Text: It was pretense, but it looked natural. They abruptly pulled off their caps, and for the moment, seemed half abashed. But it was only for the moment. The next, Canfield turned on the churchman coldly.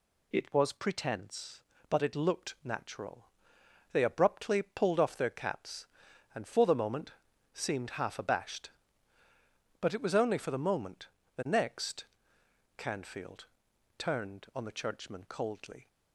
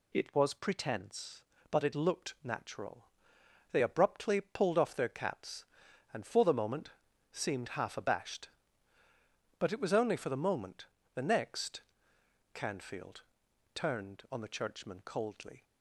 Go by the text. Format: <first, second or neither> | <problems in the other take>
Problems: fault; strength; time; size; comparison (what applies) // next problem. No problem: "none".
neither | pauses between "Canfield" and "turned"; noticeable; the same in both